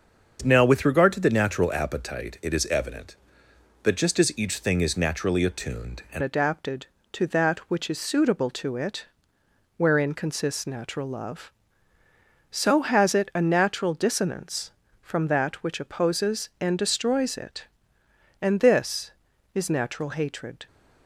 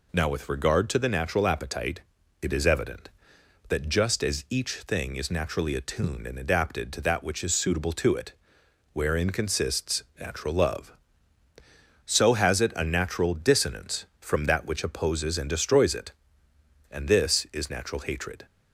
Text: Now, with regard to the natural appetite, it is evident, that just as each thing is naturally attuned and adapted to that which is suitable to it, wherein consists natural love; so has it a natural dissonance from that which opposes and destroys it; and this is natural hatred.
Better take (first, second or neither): second